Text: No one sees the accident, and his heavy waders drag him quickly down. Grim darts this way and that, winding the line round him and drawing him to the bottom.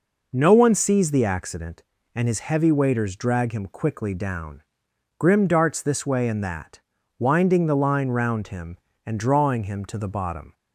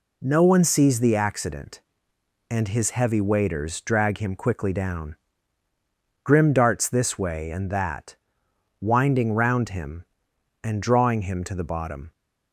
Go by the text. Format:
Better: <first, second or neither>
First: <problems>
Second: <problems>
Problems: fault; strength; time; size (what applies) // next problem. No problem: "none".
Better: first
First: none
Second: skips "the line"; at 9.3 s